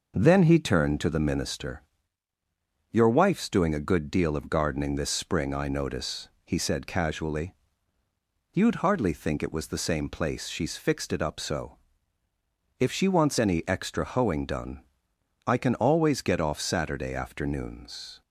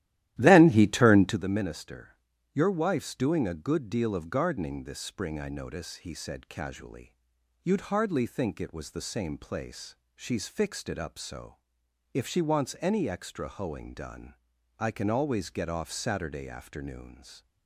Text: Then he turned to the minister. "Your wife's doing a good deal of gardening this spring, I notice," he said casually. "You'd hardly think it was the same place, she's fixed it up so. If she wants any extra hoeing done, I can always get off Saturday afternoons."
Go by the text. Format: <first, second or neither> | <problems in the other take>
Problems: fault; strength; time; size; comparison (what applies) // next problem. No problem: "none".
first | starts louder than the rest; strong; until 1.4 s; 13.5 dB